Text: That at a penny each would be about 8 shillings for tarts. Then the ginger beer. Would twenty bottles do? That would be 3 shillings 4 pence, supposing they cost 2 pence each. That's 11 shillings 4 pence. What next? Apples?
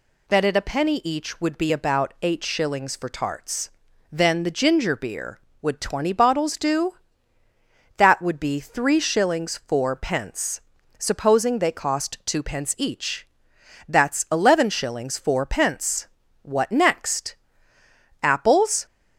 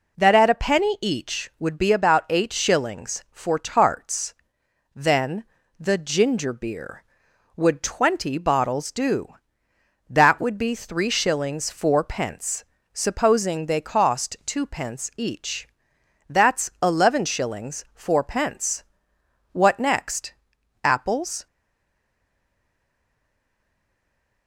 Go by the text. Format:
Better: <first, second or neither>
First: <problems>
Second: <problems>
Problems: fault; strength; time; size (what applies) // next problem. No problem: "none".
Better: first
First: none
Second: pauses between "Then" and "the"; slight; at 5.4 s; 0.36 s long // stays silent after the last word; strong; from 21.4 s on; 3.0 s long